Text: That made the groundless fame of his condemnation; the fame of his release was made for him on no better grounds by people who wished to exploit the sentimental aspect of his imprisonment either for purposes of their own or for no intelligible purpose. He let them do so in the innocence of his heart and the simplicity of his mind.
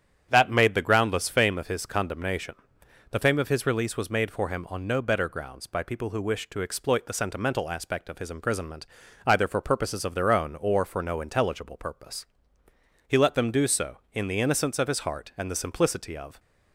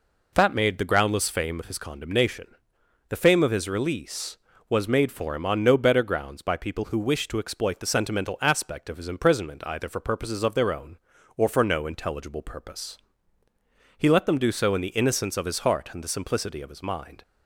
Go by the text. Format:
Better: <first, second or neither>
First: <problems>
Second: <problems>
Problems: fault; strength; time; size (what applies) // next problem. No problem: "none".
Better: second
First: starts louder than the rest; strong; until 1.3 s; 9.5 dB // pauses between "imprisonment" and "either"; at 8.8 s; 0.40 s long // stops before "his mind"; at 16.3 s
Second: none